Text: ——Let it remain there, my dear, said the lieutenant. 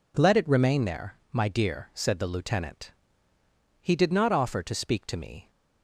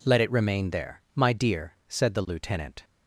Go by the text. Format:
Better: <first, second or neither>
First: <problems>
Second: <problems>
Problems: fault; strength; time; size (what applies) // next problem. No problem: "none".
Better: second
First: goes on to say "He did not offer to speak to me"; strong; from 3.8 s on; 1.7 s long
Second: none